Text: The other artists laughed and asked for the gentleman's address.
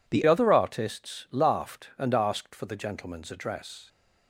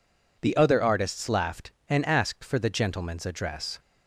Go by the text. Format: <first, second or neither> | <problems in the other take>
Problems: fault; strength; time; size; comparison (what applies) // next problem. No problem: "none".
second | changes voice at "other"; from 0.2 s on; 3.6 s long